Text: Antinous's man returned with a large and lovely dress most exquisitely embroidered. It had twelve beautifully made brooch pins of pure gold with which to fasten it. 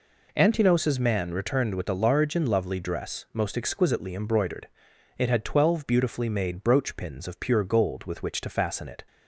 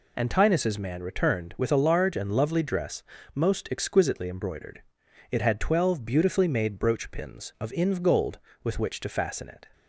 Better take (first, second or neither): first